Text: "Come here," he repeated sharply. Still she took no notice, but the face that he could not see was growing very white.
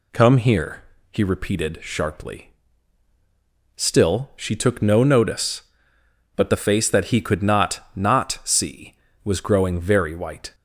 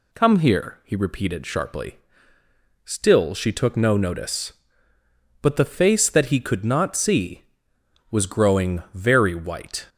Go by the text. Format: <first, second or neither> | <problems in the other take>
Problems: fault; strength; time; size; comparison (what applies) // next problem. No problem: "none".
second | says "not" twice; at 7.9 s